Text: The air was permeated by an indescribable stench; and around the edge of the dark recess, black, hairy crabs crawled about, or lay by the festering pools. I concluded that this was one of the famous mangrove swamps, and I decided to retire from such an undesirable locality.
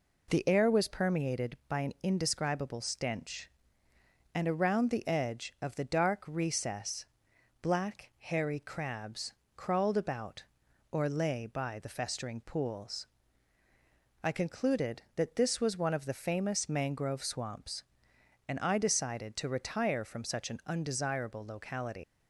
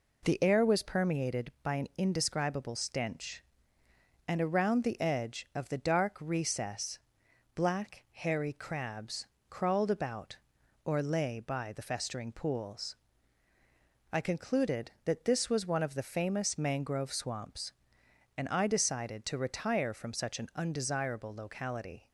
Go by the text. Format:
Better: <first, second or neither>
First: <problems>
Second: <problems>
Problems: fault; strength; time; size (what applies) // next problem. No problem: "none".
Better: second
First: pauses between "crabs" and "crawled"; slight; at 9.3 s; 0.22 s long // leaves "locality" unfinished; at 22.0 s; 180 ms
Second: pauses between "crabs" and "crawled"; slight; at 9.2 s; 0.22 s long